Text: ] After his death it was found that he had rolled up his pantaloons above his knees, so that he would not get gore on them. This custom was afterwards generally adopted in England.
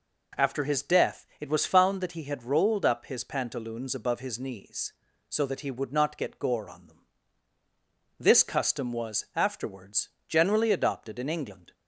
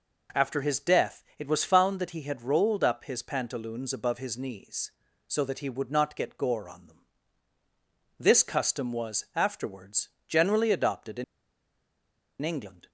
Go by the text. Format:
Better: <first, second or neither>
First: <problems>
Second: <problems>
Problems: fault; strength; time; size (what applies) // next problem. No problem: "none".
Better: first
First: pauses between "afterwards" and "generally"; slight; at 10.0 s; 0.18 s long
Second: pauses between "death" and "it"; slight; at 1.2 s; 0.16 s long // pauses between "afterwards" and "generally"; slight; at 10.0 s; 0.18 s long // pauses between "in" and "England"; at 11.2 s; 1.1 s long